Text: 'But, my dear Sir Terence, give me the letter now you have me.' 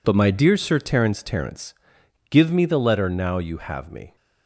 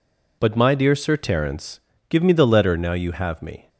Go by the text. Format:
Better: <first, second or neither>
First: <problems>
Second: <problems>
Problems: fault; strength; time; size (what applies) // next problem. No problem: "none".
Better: second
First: says "Terence" twice; at 1.2 s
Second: none